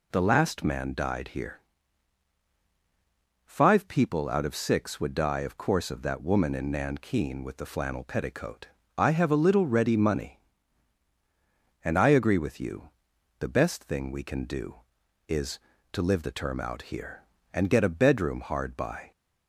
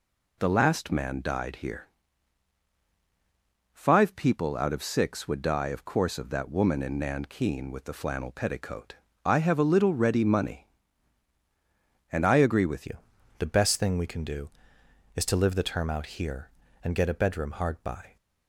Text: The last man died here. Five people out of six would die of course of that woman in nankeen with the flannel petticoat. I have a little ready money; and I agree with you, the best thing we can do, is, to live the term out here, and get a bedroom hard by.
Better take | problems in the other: first | changes voice at "you"; from 12.8 s on; 5.3 s long

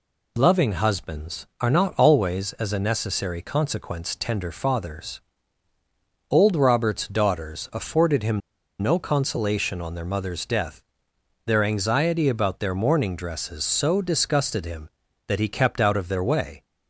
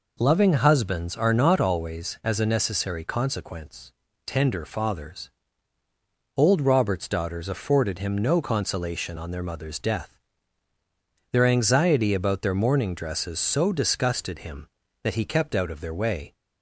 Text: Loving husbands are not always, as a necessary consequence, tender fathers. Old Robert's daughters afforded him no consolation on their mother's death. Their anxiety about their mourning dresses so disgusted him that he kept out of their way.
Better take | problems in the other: second | pauses between "him" and "no"; at 8.4 s; 0.41 s long

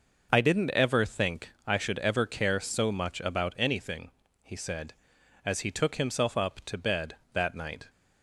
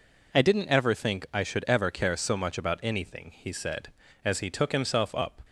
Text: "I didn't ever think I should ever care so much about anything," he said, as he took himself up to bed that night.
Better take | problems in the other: first | stops before "to bed that night"; at 5.4 s

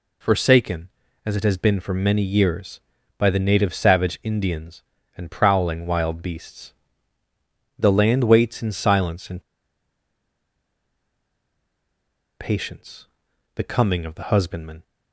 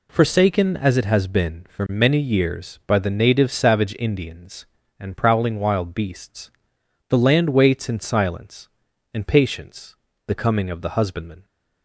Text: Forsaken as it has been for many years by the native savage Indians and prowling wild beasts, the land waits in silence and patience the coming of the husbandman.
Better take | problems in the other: second | pauses between "and" and "patience"; strong; at 9.4 s; 2.9 s long // pauses between "patience" and "the"; noticeable; at 13.0 s; 0.50 s long; slight in the second

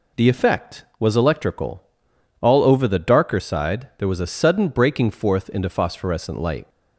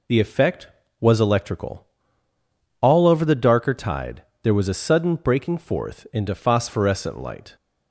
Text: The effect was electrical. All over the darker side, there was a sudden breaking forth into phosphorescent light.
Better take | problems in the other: first | says "tide" for "side"; at 3.7 s

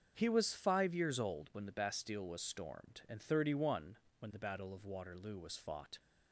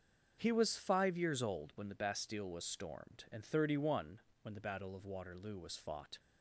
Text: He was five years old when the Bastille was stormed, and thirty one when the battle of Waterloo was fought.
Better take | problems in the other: neither | starts louder than the rest; the same in both // pauses between "one" and "when"; slight; the same in both

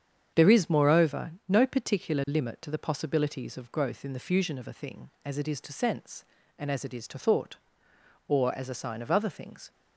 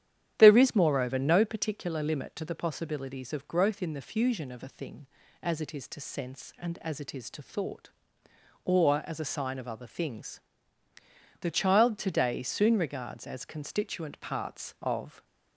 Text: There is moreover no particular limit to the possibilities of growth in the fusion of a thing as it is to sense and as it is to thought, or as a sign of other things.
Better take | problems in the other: first | starts louder than the rest; strong; until 1.3 s; 10.5 dB; strong in the first // goes on to say "The child today soon regards as constituent parts of"; strong; from 11.3 s on; 3.8 s long

